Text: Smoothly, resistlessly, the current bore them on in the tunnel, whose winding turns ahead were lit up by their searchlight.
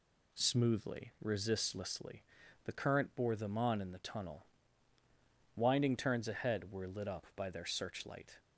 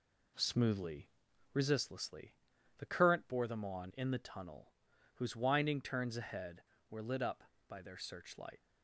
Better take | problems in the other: second | skips "whose"; at 5.0 s

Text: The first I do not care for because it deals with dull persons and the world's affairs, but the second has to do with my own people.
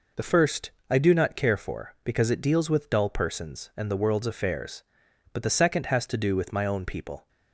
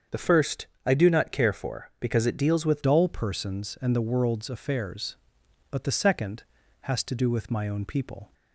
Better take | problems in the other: first | starts louder than the rest; strong; until 1.3 s; 7 dB // pauses between "first" and "I"; slight; at 0.6 s; 0.18 s long; slight in the first // changes voice at "dull"; from 2.8 s on; 5.5 s long

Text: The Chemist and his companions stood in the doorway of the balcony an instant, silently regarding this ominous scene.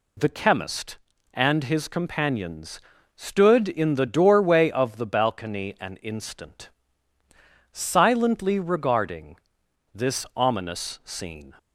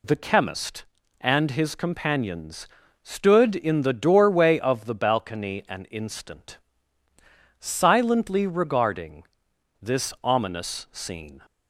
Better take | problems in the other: neither | pauses between "companions" and "stood"; slight; the same in both // pauses between "regarding" and "this"; noticeable; the same in both

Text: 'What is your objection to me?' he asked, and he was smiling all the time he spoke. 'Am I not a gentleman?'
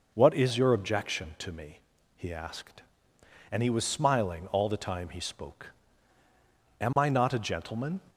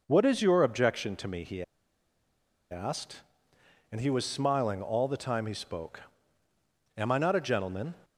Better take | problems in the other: first | pauses between "he" and "asked"; at 1.6 s; 1.0 s long

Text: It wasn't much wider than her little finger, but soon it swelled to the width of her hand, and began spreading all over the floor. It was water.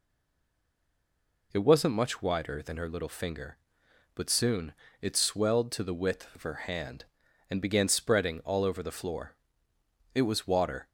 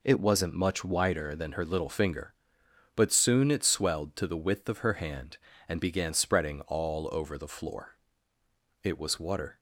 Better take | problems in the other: second | stays silent before the first word; noticeable; until 1.5 s; 1.5 s long // pauses between "soon" and "it"; slight; at 4.7 s; 0.26 s long

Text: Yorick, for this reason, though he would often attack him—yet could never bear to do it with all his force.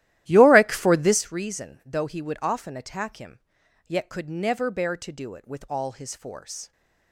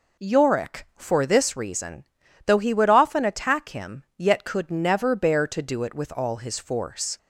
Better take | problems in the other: second | starts louder than the rest; strong; until 1.4 s; 14 dB

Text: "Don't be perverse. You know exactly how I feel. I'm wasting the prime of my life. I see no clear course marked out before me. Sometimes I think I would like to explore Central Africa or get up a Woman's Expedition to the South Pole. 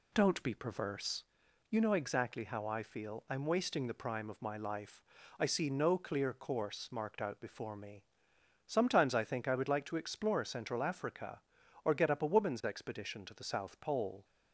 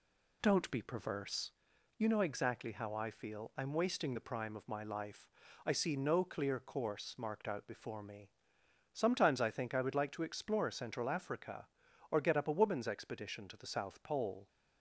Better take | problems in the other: neither | none

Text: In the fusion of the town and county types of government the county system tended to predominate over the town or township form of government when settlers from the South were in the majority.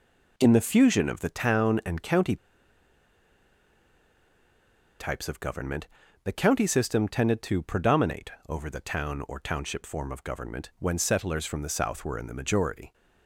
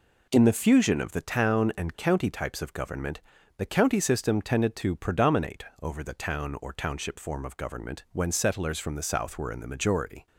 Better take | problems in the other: second | pauses between "county" and "types"; strong; at 2.3 s; 2.6 s long // pauses between "government" and "the"; at 5.8 s; 0.38 s long; also in the second // pauses between "predominate" and "over"; slight; at 8.3 s; 0.18 s long; slight in the second

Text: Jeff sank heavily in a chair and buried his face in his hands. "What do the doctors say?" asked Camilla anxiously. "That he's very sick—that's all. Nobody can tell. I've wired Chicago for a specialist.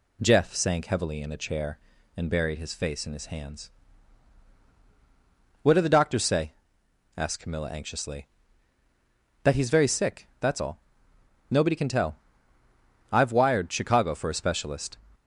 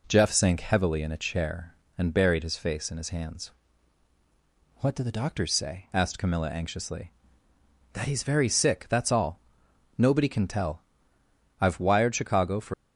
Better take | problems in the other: first | stops before "a specialist"; at 12.7 s

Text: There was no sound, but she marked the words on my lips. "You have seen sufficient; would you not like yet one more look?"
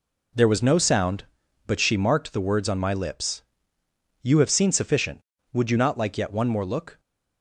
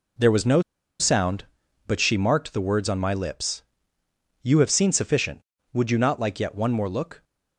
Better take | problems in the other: first | pauses between "no" and "sound"; at 0.6 s; 0.37 s long

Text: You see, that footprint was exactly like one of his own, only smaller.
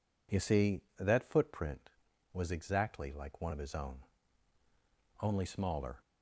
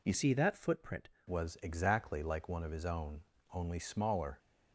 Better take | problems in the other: first | changes voice from "see" to "footprint"; from 0.1 to 1.0 s; 0.9 s long

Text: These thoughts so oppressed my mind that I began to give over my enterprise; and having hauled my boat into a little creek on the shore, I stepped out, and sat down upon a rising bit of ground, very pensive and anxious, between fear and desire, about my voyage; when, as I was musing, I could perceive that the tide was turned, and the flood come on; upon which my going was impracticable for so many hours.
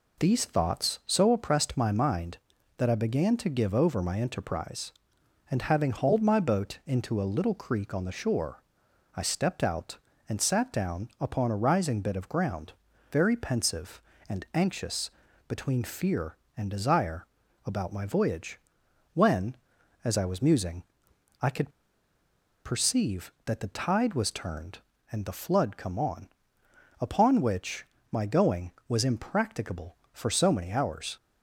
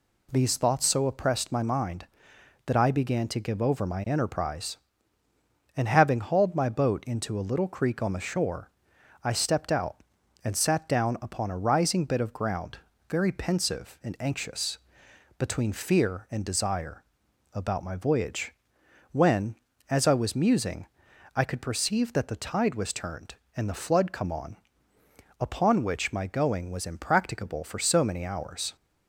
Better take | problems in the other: second | pauses between "could" and "perceive"; noticeable; at 21.7 s; 0.94 s long // pauses between "which" and "my"; slight; at 27.8 s; 0.26 s long

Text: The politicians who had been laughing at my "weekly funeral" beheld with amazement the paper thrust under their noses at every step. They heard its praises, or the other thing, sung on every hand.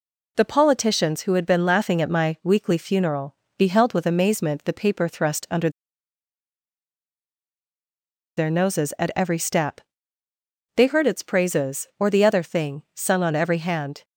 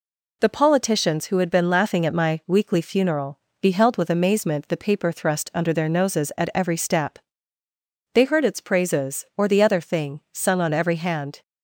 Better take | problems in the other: second | pauses between "funeral" and "beheld"; slight; at 3.3 s; 0.22 s long; slight in the second // pauses between "under" and "their"; strong; at 5.6 s; 2.6 s long

